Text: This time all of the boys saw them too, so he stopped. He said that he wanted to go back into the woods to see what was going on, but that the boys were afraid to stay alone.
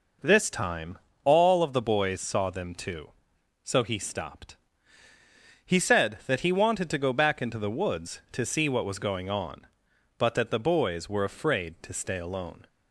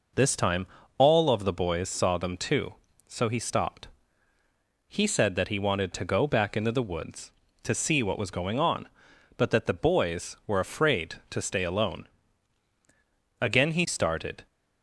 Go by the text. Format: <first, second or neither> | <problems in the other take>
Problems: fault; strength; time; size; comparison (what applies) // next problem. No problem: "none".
first | pauses between "time" and "all"; slight; at 0.6 s; 0.32 s long; slight in the first // goes on to say "Again he started"; noticeable; from 13.4 s on; 1.0 s long